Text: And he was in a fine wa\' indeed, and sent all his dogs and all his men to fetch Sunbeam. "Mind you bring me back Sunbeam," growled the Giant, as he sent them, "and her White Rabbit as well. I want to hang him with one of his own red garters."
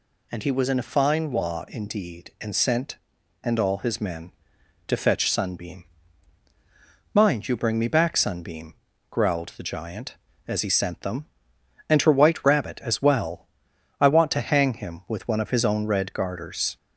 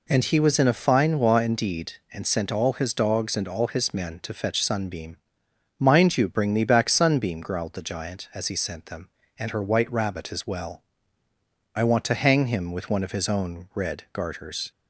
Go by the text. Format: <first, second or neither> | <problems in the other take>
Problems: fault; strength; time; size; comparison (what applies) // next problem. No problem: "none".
second | skips "all his dogs"; at 3.1 s